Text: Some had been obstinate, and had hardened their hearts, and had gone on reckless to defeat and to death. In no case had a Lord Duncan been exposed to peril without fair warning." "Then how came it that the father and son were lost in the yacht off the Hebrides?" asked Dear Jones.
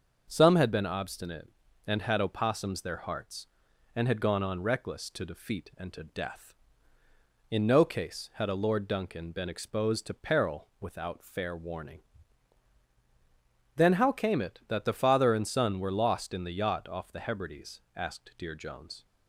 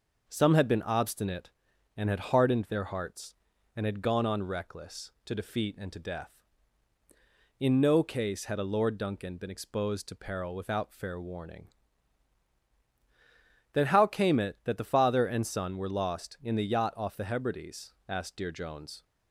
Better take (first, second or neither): second